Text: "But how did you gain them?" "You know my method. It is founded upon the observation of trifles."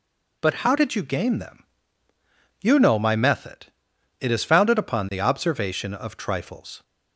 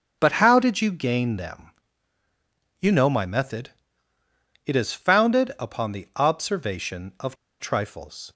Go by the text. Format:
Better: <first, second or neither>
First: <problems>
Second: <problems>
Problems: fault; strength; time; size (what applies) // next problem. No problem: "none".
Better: first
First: none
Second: starts louder than the rest; strong; until 1.2 s; 7.5 dB // pauses between "of" and "trifles"; slight; at 7.3 s; 0.24 s long